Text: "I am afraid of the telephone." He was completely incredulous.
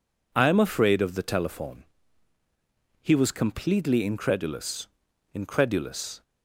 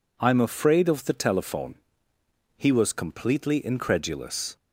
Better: second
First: says "incredulous" twice; at 5.3 s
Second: none

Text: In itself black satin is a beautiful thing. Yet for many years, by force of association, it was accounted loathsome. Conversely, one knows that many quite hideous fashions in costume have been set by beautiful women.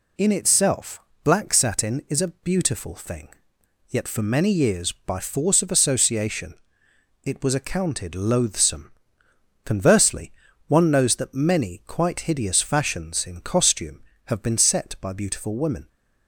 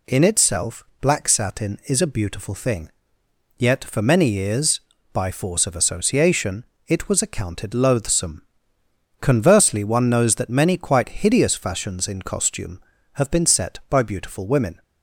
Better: neither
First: pauses between "itself" and "black"; slight; at 0.9 s; 0.24 s long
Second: pauses between "itself" and "black"; slight; at 0.8 s; 0.18 s long

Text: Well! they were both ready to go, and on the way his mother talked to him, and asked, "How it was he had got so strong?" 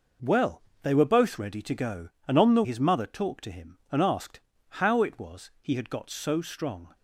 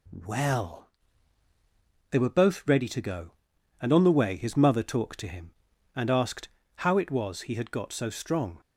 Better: second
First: skips "way"; at 2.6 s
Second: none

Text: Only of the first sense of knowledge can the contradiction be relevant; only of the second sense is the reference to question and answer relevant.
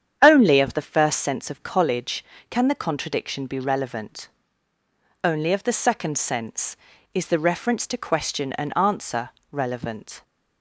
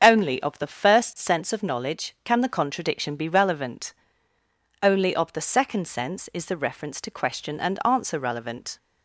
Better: second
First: starts louder than the rest; strong; until 1.2 s; 8.5 dB // says "college" for "knowledge"; at 1.6 s // pauses between "answer" and "relevant"; slight; at 9.2 s; 0.24 s long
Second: starts louder than the rest; strong; until 1.0 s; 7 dB

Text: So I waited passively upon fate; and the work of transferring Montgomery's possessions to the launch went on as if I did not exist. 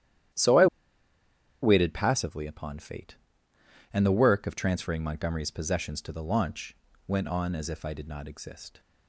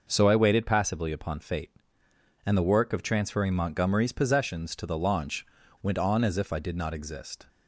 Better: second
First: starts louder than the rest; strong; until 2.3 s; 11.5 dB // pauses between "I" and "waited"; noticeable; at 0.6 s; 0.96 s long // pauses between "launch" and "went"; slight; at 6.7 s; 0.32 s long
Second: pauses between "launch" and "went"; at 5.4 s; 0.38 s long

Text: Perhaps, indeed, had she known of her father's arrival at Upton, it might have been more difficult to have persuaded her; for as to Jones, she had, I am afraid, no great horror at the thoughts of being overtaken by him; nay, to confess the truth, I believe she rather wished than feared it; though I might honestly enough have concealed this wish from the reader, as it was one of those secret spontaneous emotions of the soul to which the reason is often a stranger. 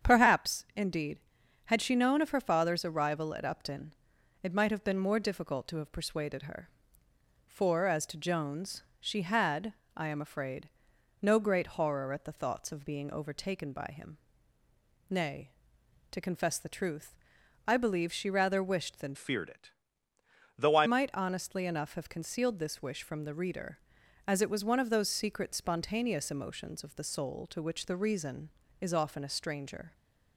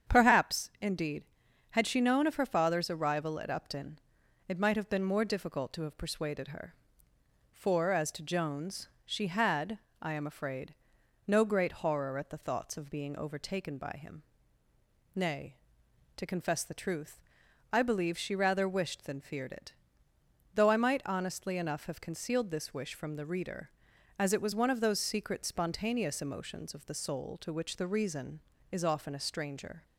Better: second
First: starts louder than the rest; strong; until 1.1 s; 8 dB // changes voice from "feared" to "I"; from 19.1 to 20.8 s; 1.7 s long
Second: starts louder than the rest; strong; until 1.1 s; 8 dB

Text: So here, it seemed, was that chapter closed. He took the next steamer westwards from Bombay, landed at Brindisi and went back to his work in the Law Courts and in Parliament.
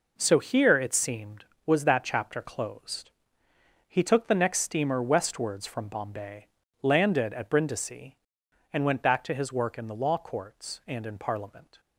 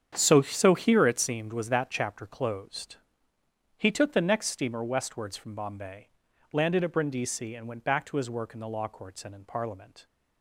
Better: first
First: none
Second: starts louder than the rest; strong; until 1.1 s; 8 dB // says "So" twice; at 0.4 s

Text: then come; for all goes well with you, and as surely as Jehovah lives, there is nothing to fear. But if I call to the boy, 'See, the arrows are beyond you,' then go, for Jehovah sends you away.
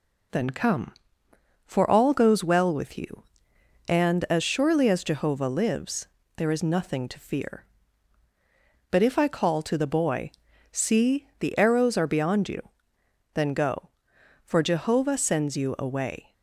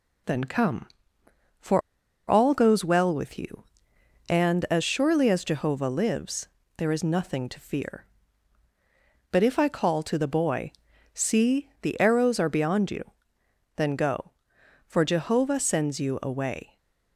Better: first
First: none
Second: pauses between "for" and "all"; noticeable; at 1.8 s; 0.49 s long

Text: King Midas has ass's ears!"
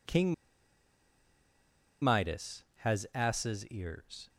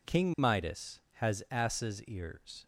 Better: second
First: pauses between "King" and "Midas"; strong; at 0.3 s; 1.6 s long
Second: none

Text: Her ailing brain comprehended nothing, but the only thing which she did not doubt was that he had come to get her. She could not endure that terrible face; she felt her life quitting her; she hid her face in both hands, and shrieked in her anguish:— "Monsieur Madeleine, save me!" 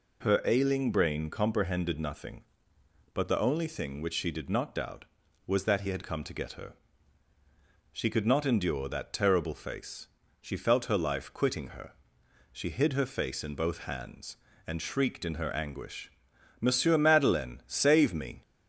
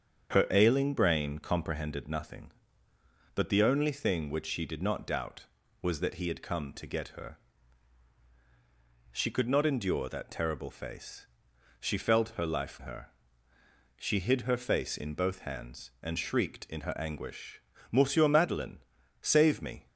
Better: first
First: none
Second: starts louder than the rest; strong; until 1.3 s; 7.5 dB // skips "quitting"; at 12.8 s

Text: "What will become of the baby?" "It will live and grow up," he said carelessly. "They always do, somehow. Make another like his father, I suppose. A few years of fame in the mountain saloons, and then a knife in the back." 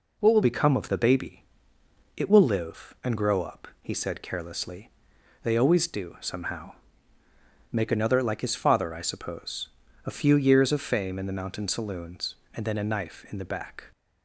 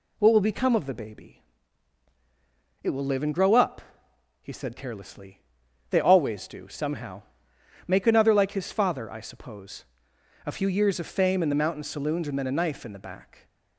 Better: second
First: changes voice at "become"; from 0.4 s on; 13.5 s long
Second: none

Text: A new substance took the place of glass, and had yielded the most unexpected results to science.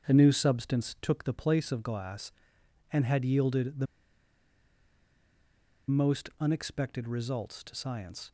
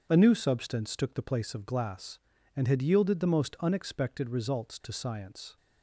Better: second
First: starts louder than the rest; strong; until 1.1 s; 7.5 dB // pauses between "the" and "most"; strong; at 3.8 s; 2.0 s long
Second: starts louder than the rest; until 1.1 s; 7 dB

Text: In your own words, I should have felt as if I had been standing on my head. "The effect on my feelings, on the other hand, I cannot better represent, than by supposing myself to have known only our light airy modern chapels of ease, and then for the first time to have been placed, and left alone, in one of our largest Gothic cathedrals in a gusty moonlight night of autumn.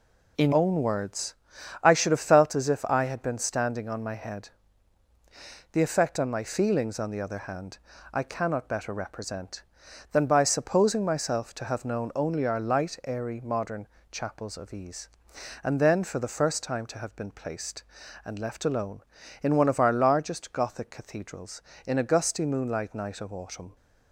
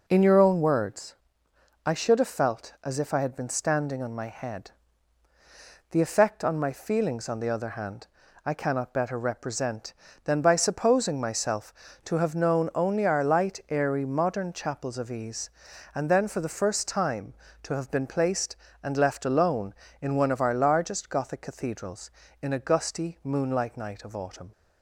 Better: second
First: skips "your"; at 0.5 s // pauses between "modern" and "chapels"; slight; at 13.8 s; 0.24 s long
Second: none

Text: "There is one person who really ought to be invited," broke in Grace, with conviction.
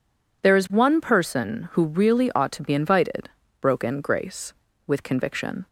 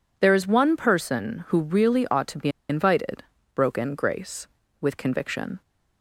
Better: first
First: none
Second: pauses between "be" and "invited"; slight; at 2.4 s; 0.21 s long

